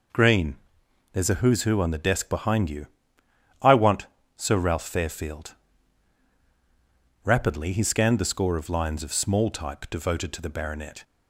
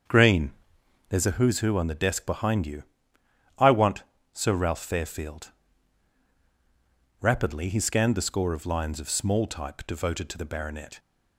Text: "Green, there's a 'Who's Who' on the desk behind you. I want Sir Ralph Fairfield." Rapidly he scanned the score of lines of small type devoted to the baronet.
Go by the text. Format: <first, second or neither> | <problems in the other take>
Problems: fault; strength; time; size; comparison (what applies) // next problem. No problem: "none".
first | starts louder than the rest; strong; until 1.3 s; 7 dB // pauses between "want" and "Sir"; slight; at 4.0 s; 0.28 s long; slight in the first